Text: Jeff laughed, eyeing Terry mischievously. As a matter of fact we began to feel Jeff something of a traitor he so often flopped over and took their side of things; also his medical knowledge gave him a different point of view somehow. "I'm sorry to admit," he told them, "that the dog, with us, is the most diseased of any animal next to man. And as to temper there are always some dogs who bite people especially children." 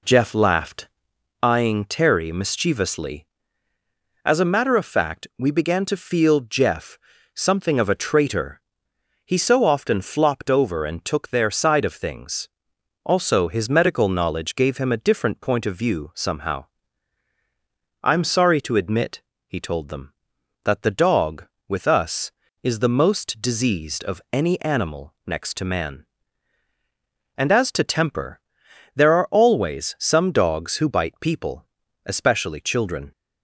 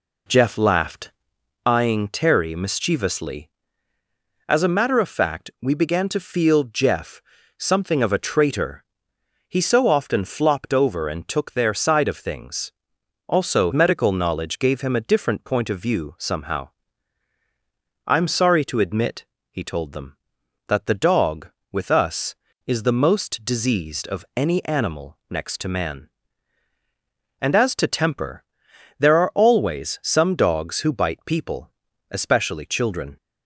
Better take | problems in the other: first | pauses between "Jeff" and "something"; at 7.2 s; 0.38 s long; also in the first // pauses between "traitor" and "he"; noticeable; at 8.8 s; 0.66 s long; noticeable in the first // skips "his"; at 13.7 s // pauses between "temper" and "there"; noticeable; at 28.4 s; 0.54 s long; noticeable in the first // pauses between "people" and "especially"; at 31.7 s; 0.40 s long; also in the first

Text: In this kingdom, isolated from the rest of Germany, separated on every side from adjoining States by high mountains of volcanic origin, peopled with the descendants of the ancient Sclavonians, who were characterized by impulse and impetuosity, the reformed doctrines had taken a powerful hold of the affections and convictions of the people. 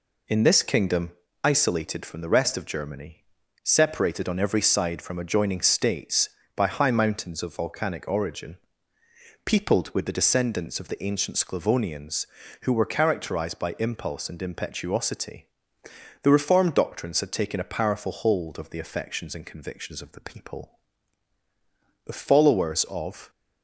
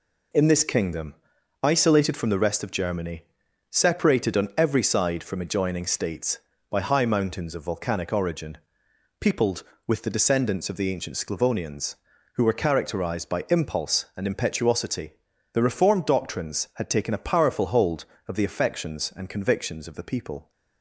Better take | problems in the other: second | goes on to say "The followers of"; noticeable; from 22.0 s on; 1.2 s long

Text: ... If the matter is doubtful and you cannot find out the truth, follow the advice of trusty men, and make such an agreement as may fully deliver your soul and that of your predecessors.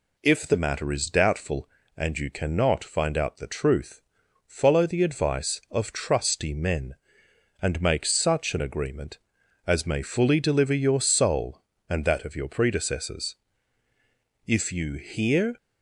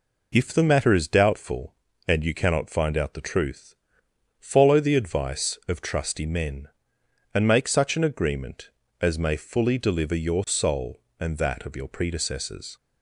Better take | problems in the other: second | goes on to say "If you hear"; noticeable; from 14.4 s on; 1.1 s long

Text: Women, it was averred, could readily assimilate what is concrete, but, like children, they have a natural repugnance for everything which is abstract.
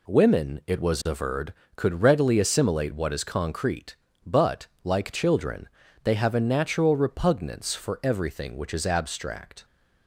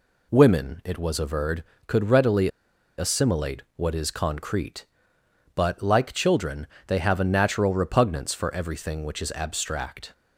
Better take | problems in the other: first | pauses between "readily" and "assimilate"; noticeable; at 2.4 s; 0.49 s long

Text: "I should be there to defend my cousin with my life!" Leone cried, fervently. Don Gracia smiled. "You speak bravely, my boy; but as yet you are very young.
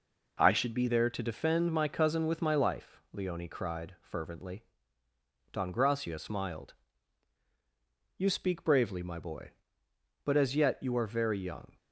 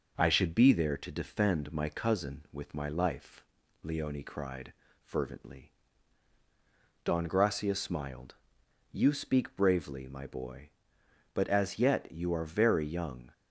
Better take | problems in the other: second | changes voice at "there"; from 0.8 s on; 10.9 s long

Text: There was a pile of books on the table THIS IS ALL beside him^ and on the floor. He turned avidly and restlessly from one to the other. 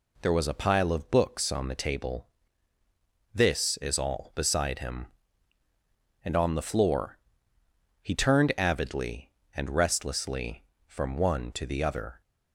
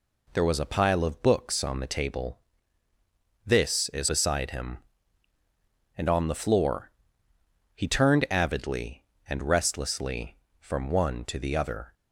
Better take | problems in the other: first | pauses between "table" and "THIS"; at 2.3 s; 1.0 s long; also in the first // skips "ALL"; at 4.0 s

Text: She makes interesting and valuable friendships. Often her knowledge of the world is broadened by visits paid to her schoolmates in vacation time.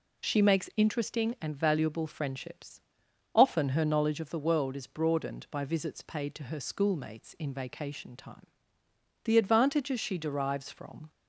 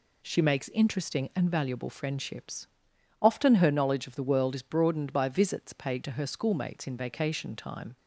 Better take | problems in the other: second | goes on to say "The advantages she derives from"; strong; from 9.2 s on; 1.8 s long

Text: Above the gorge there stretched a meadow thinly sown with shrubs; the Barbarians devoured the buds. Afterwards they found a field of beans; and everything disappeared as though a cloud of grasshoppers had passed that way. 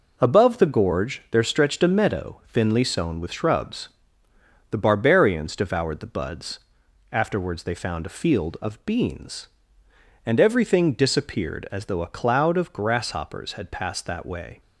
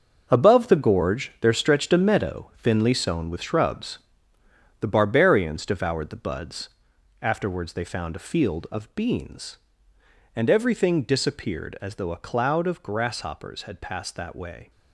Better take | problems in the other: first | gets quieter; strong; throughout; 10.5 dB

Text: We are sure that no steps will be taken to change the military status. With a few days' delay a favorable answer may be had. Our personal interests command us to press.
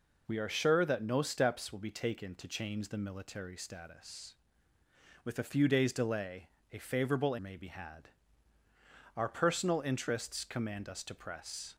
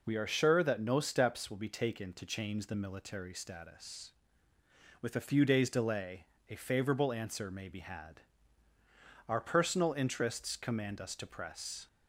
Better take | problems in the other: second | pauses between "delay" and "a"; slight; at 6.4 s; 0.24 s long; slight in the second // skips "answer"; at 7.3 s

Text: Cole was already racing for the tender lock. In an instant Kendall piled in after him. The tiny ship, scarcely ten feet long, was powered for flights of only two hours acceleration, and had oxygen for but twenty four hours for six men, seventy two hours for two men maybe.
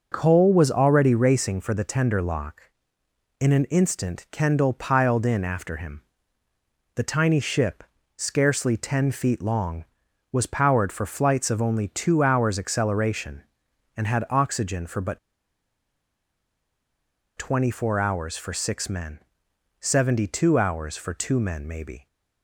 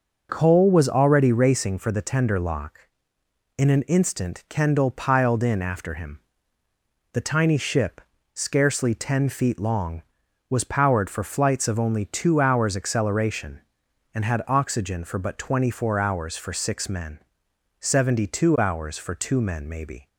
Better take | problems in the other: second | starts louder than the rest; until 1.1 s; 6 dB; also in the second // pauses between "but" and "twenty"; strong; at 15.1 s; 2.1 s long

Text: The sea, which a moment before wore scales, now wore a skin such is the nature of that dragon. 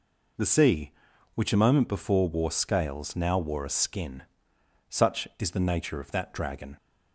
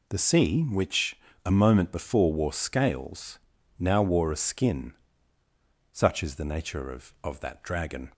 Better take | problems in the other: first | pauses between "which" and "a"; slight; at 1.1 s; 0.24 s long // pauses between "skin" and "such"; noticeable; at 4.9 s; 0.96 s long; noticeable in the first // says "of" twice; at 7.2 s

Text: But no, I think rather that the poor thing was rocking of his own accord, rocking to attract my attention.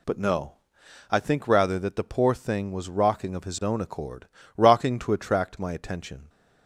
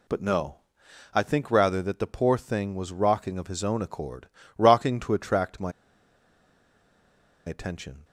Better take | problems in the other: first | pauses between "my" and "attention"; strong; at 5.7 s; 1.7 s long

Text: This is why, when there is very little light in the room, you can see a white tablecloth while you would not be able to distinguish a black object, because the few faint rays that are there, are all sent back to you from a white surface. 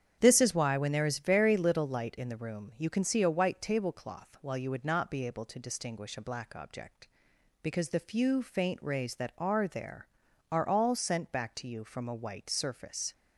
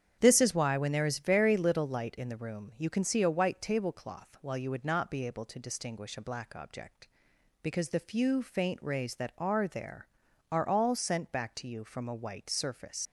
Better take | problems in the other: first | starts louder than the rest; strong; until 1.2 s; 8.5 dB; strong in the first // leaves "surface" unfinished; at 13.0 s; 70 ms

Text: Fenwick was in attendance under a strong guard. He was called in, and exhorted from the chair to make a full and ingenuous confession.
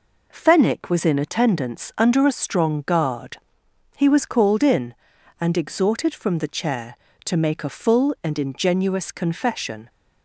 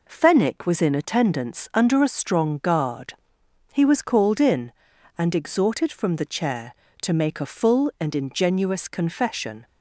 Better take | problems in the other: neither | none

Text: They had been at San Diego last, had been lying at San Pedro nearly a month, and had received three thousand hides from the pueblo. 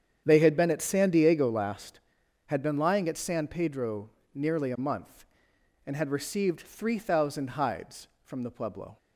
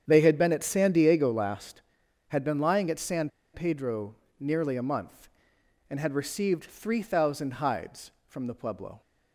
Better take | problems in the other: first | starts louder than the rest; strong; until 1.0 s; 8.5 dB; strong in the first // pauses between "San" and "Pedro"; slight; at 3.2 s; 0.24 s long // pauses between "Pedro" and "nearly"; slight; at 4.1 s; 0.24 s long; slight in the first

